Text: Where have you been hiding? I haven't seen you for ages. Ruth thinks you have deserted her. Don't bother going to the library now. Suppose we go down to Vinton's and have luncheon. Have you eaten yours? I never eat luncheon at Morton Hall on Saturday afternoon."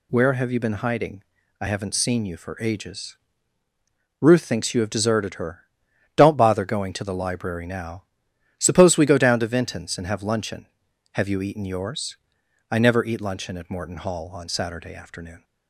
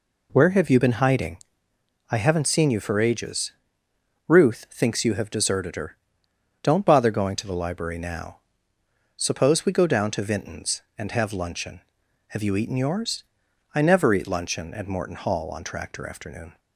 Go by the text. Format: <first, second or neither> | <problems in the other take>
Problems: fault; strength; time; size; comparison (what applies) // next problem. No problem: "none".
first | says "Tractor" for "Saturday"; at 15.6 s